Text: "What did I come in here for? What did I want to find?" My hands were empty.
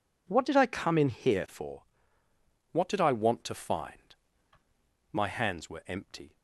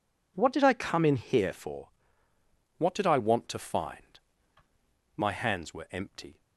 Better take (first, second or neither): neither